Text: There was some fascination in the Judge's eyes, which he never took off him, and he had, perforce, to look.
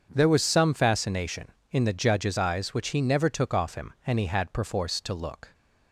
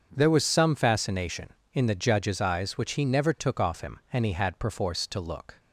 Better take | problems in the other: neither | starts louder than the rest; the same in both

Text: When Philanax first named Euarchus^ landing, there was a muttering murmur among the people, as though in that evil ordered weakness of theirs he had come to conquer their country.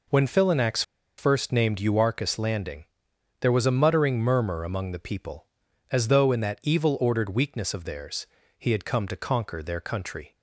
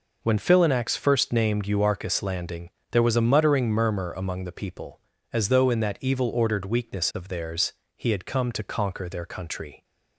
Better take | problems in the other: second | pauses between "Philanax" and "first"; at 0.8 s; 0.36 s long // pauses between "theirs" and "he"; slight; at 8.2 s; 0.32 s long; slight in the second

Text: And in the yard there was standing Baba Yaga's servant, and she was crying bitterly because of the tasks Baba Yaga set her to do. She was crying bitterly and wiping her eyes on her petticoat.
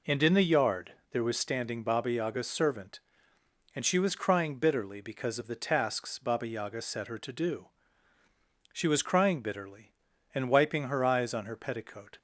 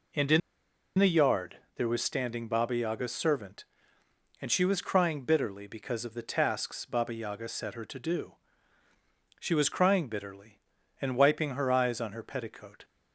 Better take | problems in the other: first | pauses between "in" and "the"; noticeable; at 0.4 s; 0.58 s long // pauses between "yard" and "there"; slight; at 1.5 s; 0.20 s long; slight in the first

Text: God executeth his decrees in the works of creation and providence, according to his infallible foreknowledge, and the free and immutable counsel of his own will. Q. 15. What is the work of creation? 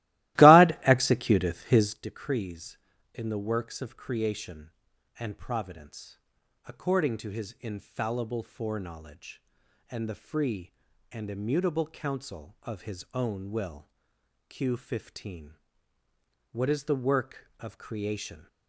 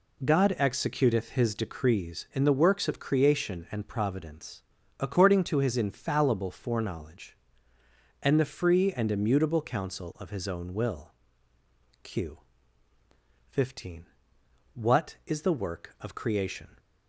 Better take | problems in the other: second | starts louder than the rest; strong; until 2.0 s; 17.5 dB

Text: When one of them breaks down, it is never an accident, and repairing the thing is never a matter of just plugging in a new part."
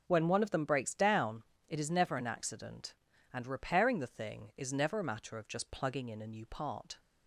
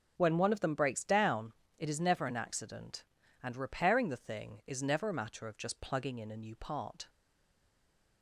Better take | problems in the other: first | stays silent after the last word; from 7.0 s on; 1.2 s long

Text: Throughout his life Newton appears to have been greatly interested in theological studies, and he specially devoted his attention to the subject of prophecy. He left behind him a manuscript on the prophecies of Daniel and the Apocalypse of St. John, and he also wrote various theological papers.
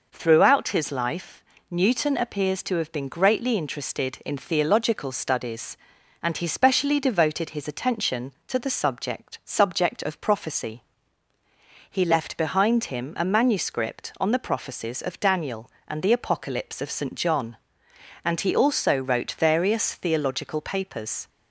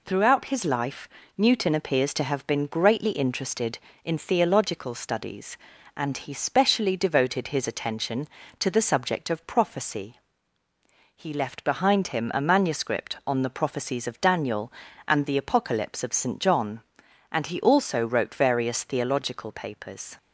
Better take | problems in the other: second | pauses between "life" and "Newton"; slight; at 1.4 s; 0.28 s long; slight in the second // says "subject" twice; at 9.4 s

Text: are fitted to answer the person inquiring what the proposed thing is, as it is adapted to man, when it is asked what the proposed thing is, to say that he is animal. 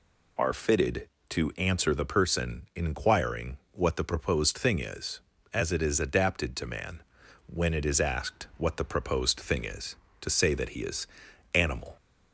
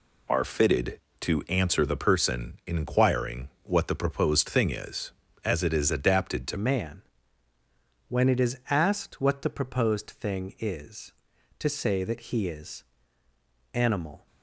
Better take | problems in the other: first | changes voice at "man"; from 6.5 s on; 7.7 s long // pauses between "is" and "animal"; noticeable; at 12.8 s; 0.90 s long; noticeable in the first

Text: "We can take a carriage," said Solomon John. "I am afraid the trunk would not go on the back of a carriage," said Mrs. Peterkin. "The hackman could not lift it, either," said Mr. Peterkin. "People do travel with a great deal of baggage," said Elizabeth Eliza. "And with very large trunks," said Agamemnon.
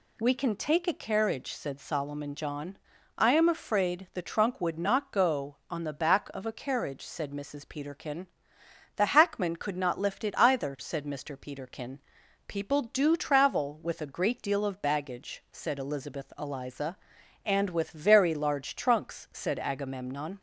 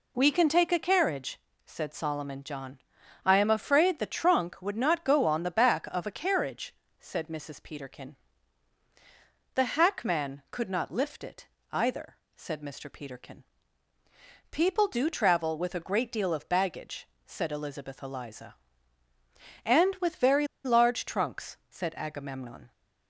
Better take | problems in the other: first | pauses between "very" and "large"; slight; at 20.4 s; 0.18 s long

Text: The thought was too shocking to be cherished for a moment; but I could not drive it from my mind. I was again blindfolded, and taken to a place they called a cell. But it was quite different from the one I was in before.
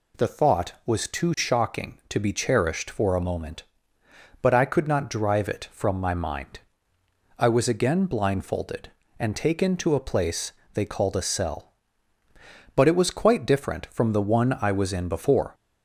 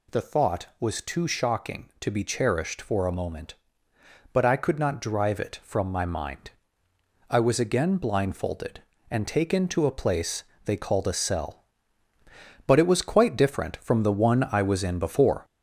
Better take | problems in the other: first | gets louder; noticeable; throughout; 4 dB // pauses between "place" and "they"; slight; at 10.4 s; 0.24 s long; slight in the first

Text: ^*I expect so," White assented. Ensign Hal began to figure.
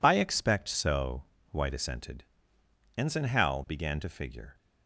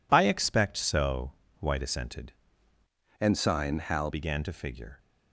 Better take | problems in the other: first | changes voice from "Ensign" to "Hal"; from 3.2 to 4.1 s; 0.9 s long

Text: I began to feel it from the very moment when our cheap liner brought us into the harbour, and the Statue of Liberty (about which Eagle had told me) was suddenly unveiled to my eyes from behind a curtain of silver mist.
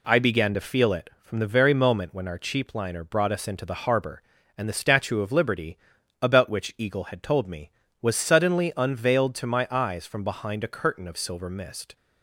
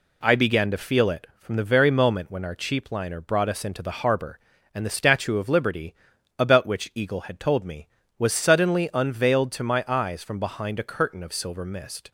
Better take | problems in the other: neither | none

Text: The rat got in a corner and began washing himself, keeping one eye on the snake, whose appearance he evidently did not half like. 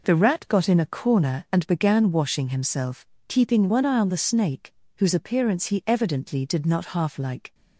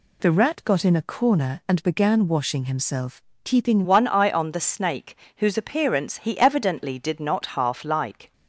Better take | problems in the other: first | changes voice at "one"; from 3.8 s on; 4.5 s long

